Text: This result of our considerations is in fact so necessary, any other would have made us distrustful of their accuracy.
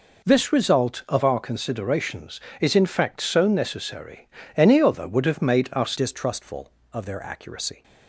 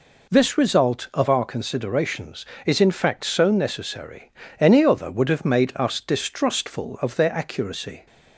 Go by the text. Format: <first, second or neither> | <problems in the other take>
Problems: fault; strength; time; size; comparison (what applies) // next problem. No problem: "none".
second | changes voice at "distrustful"; from 5.9 s on; 1.9 s long